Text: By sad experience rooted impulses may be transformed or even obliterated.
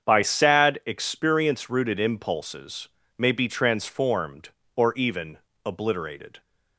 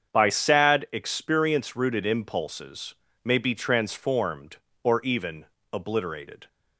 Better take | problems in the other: neither | starts louder than the rest; strong; the same in both // pauses between "impulses" and "may"; slight; the same in both // pauses between "even" and "obliterated"; slight; the same in both

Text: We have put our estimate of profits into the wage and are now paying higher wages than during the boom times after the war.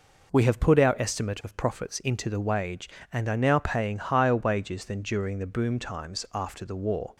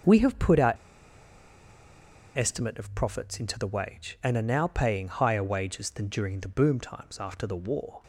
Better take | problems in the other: first | starts louder than the rest; until 2.6 s; 6 dB // pauses between "our" and "estimate"; strong; at 0.7 s; 1.6 s long

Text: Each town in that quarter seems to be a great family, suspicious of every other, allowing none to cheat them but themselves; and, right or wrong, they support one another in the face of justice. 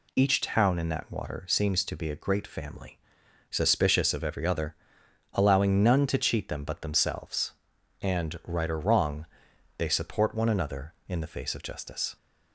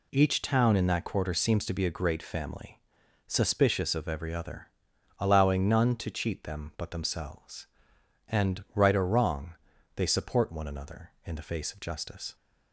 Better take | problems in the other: second | says "water" for "quarter"; at 1.1 s

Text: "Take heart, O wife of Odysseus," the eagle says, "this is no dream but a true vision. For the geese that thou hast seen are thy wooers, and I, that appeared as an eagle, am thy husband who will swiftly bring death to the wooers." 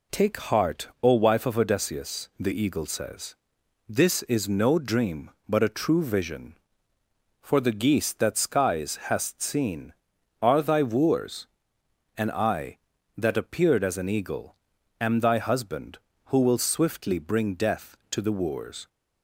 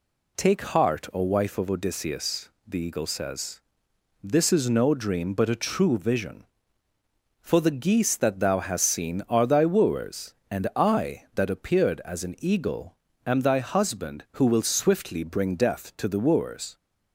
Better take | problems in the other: second | says "skies" for "thou"; at 8.3 s

